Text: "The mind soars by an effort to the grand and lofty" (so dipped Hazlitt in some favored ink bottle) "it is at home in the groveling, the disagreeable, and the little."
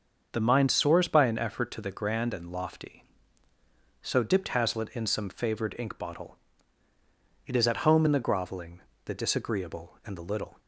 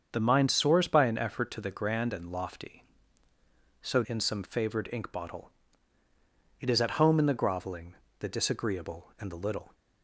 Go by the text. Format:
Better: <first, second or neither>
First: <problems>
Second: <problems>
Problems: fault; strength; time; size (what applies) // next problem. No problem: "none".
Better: first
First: starts louder than the rest; until 1.3 s; 6.5 dB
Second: starts louder than the rest; until 1.1 s; 7 dB // skips "dipped Hazlitt"; at 4.0 s